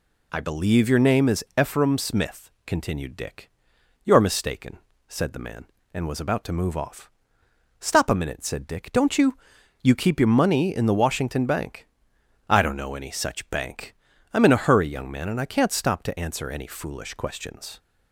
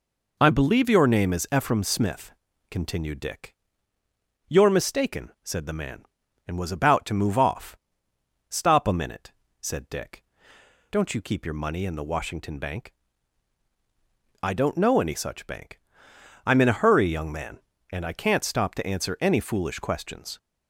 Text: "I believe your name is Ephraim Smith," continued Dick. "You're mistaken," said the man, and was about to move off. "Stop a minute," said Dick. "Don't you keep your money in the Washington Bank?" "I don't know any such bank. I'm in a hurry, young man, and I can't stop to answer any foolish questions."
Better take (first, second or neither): second